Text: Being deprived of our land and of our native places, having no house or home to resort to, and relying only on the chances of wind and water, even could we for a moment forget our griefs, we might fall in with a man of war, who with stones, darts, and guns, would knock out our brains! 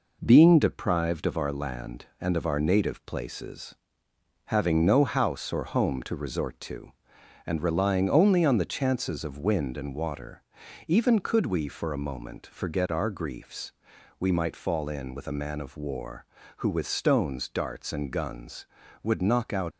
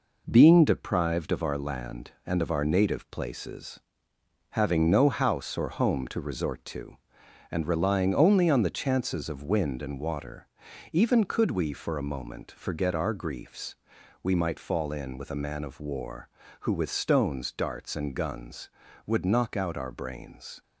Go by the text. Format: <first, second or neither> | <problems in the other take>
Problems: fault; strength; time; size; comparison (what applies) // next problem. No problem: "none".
second | stops before "our brains"; at 19.7 s